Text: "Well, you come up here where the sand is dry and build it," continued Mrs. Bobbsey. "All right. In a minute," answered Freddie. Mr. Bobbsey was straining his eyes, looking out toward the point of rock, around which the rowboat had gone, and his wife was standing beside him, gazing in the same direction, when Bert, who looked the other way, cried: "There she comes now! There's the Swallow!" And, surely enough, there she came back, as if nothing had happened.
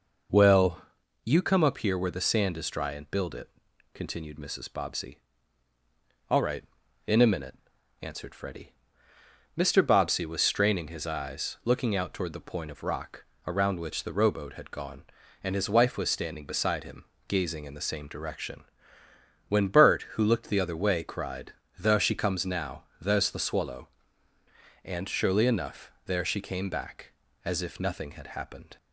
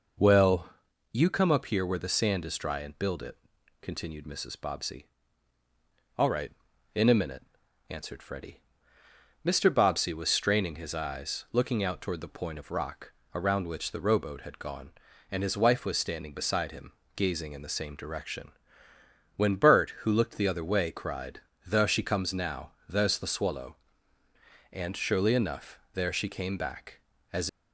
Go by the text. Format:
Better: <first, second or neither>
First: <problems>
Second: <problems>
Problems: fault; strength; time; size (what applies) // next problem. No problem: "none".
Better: first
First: none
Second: stops before "if nothing had happened"; at 27.4 s